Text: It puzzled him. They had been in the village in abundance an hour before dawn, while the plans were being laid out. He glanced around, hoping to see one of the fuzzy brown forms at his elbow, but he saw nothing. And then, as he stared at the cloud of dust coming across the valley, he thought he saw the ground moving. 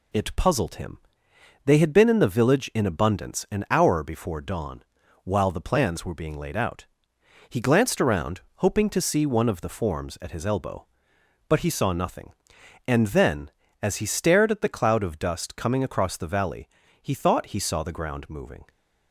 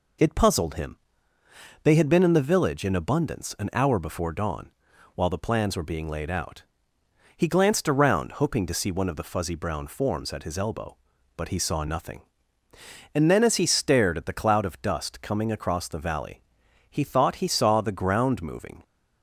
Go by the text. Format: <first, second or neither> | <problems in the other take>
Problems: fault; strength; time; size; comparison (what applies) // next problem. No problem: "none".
second | skips "fuzzy brown"; at 9.6 s